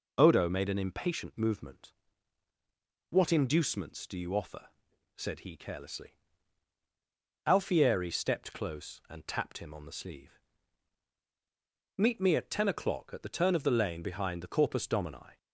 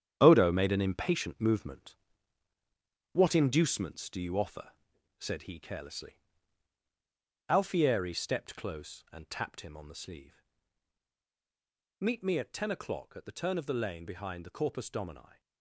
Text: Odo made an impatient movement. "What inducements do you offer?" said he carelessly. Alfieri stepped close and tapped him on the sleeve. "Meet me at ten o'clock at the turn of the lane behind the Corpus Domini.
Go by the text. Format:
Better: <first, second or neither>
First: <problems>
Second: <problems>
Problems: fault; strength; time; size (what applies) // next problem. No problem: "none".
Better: first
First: none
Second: gets quieter; strong; throughout; 9.5 dB